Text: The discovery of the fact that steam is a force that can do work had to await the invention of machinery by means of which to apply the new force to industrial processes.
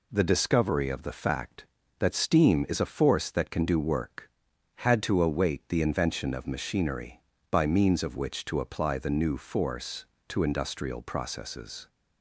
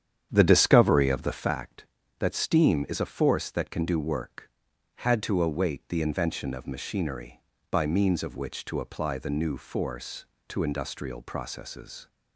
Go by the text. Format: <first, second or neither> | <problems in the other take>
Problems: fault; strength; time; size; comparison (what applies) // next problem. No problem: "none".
first | starts louder than the rest; strong; until 1.5 s; 9 dB